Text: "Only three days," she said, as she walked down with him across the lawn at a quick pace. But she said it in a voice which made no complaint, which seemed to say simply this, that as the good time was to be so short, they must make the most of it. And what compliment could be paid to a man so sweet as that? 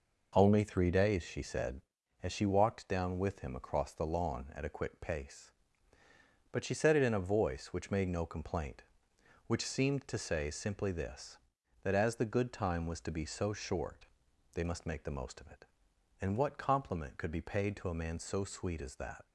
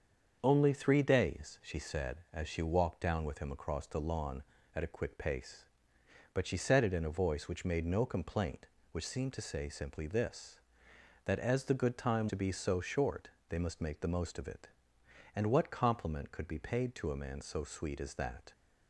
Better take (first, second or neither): first